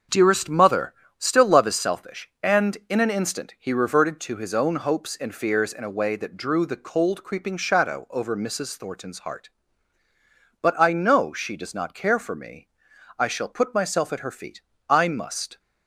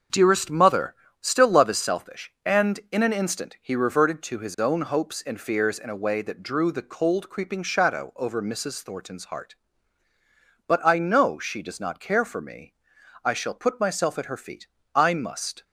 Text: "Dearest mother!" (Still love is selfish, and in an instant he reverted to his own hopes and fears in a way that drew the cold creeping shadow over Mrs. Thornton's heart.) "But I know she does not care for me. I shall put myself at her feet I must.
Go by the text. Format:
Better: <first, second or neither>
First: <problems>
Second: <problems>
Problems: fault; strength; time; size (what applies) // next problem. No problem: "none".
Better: neither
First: starts louder than the rest; until 1.3 s; 6.5 dB // pauses between "feet" and "I"; slight; at 14.6 s; 0.26 s long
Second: starts louder than the rest; until 1.3 s; 6.5 dB // pauses between "feet" and "I"; slight; at 14.6 s; 0.26 s long